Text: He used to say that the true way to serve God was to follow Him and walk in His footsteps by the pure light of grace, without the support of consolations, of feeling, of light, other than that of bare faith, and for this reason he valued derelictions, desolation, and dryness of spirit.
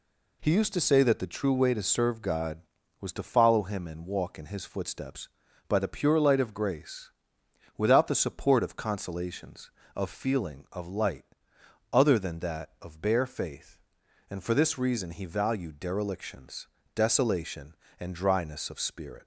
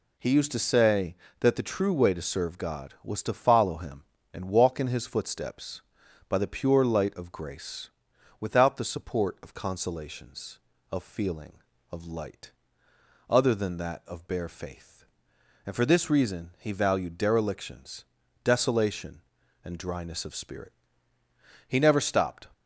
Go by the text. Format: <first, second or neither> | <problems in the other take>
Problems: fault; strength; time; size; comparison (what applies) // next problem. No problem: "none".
first | goes on to say "He never stopped"; noticeable; from 21.6 s on; 0.80 s long